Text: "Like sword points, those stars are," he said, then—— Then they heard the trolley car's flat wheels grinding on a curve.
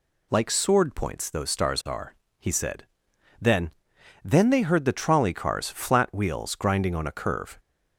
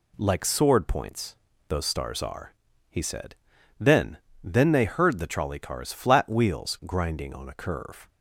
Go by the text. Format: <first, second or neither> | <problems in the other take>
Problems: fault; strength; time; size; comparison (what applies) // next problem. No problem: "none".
neither | none